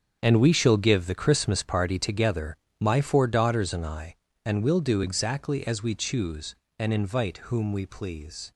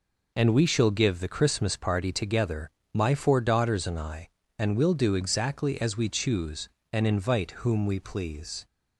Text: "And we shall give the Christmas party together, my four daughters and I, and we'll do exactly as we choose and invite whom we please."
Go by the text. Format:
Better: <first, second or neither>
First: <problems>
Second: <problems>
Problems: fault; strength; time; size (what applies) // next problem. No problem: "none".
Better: second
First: gets quieter; strong; throughout; 12 dB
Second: none